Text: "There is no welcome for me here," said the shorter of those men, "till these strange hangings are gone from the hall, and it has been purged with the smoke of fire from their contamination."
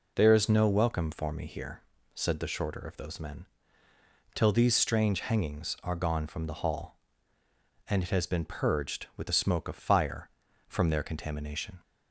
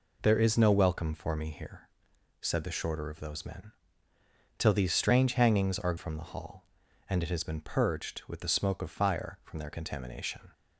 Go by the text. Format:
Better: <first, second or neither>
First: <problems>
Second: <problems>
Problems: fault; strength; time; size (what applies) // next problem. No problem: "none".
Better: first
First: none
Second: skips "gone"; at 5.9 s